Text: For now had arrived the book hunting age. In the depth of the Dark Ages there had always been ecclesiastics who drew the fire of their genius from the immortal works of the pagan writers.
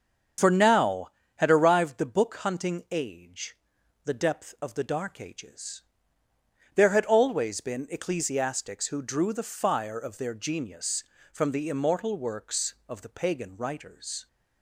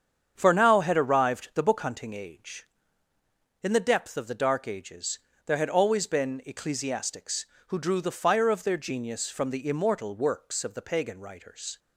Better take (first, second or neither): second